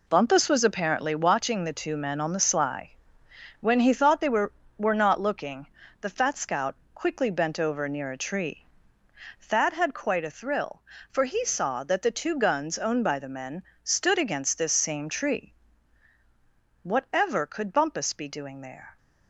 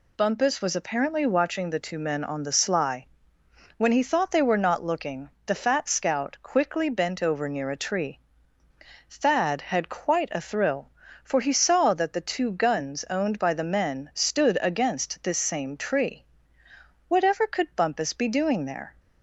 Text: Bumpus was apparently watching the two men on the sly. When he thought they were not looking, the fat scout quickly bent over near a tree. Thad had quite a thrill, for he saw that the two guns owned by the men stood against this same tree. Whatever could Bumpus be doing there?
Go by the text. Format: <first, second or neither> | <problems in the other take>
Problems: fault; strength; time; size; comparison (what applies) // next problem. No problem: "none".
second | says "were" twice; at 4.7 s // pauses between "scout" and "quickly"; slight; at 6.7 s; 0.18 s long // pauses between "men" and "stood"; slight; at 13.6 s; 0.20 s long